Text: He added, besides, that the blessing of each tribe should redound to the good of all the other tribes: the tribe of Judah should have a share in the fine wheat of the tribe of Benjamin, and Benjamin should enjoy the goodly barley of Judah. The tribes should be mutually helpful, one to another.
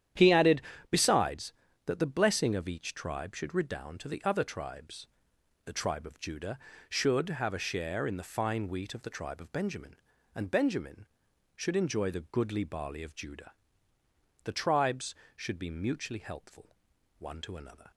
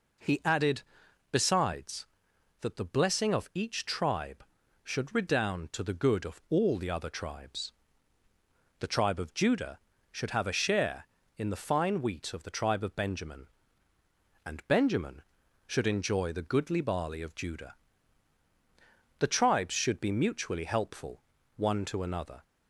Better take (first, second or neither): second